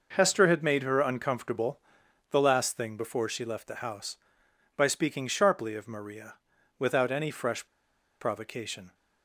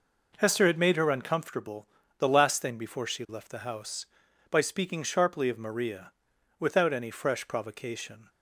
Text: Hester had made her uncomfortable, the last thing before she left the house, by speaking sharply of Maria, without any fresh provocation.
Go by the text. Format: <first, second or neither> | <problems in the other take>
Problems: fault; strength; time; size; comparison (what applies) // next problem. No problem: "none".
second | pauses between "fresh" and "provocation"; noticeable; at 7.6 s; 0.55 s long